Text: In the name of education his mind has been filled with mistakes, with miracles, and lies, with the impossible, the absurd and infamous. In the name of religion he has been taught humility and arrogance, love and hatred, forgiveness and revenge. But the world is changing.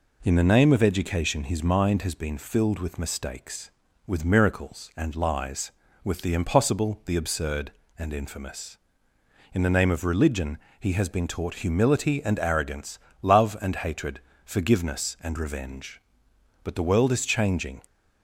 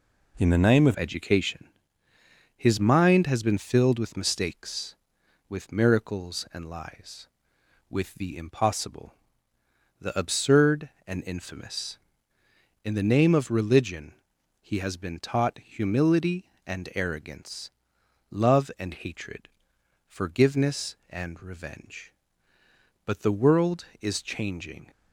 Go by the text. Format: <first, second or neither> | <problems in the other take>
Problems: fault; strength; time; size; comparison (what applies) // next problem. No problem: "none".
first | changes voice at "education"; from 0.9 s on; 23.9 s long // pauses between "education" and "his"; noticeable; at 1.6 s; 0.90 s long // pauses between "religion" and "he"; noticeable; at 14.1 s; 0.48 s long; slight in the first